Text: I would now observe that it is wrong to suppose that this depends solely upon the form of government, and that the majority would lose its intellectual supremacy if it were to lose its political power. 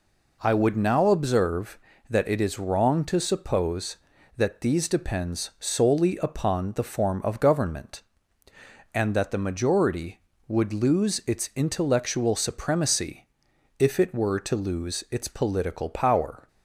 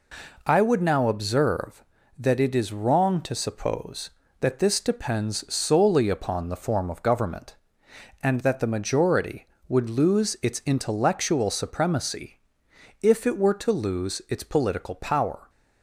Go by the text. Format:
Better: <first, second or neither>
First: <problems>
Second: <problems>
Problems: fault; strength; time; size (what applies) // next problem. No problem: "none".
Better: second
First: says "these" for "this"; at 4.6 s // pauses between "supremacy" and "if"; noticeable; at 13.2 s; 0.52 s long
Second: pauses between "supremacy" and "if"; noticeable; at 12.3 s; 0.62 s long